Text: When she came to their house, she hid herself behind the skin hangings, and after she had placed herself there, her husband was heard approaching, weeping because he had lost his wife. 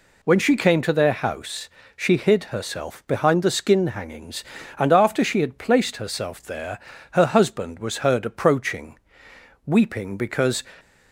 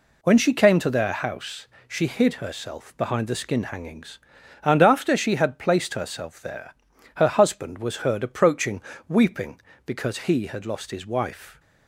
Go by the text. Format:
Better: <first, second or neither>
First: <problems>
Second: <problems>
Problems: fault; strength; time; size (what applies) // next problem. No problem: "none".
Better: second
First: stops before "he had lost his wife"; at 10.7 s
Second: none